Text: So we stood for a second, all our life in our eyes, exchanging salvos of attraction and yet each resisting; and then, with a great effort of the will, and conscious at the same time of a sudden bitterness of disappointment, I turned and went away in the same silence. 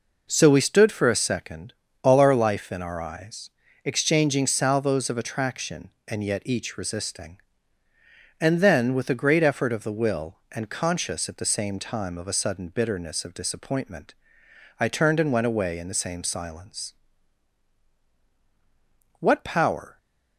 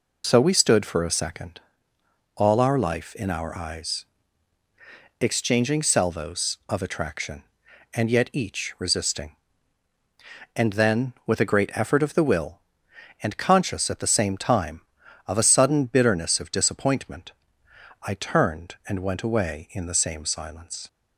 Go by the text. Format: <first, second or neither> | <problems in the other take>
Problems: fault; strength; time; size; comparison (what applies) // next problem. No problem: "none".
second | goes on to say "What power"; noticeable; from 19.2 s on; 0.76 s long